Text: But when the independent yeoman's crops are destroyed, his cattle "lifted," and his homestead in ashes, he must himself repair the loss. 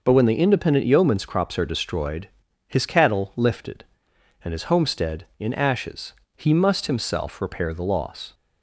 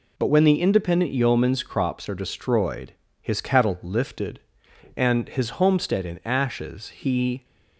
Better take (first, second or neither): first